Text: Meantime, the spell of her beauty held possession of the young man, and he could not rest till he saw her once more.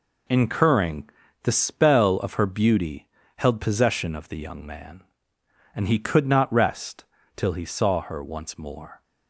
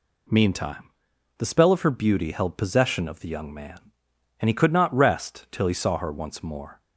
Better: second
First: says "Incurring" for "Meantime"; at 0.2 s // pauses between "beauty" and "held"; slight; at 3.0 s; 0.30 s long // pauses between "rest" and "till"; slight; at 7.0 s; 0.32 s long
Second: none

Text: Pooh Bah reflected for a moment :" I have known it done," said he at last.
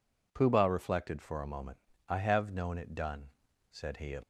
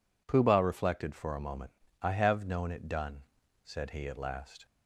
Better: second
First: stops before "last"; at 4.2 s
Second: none

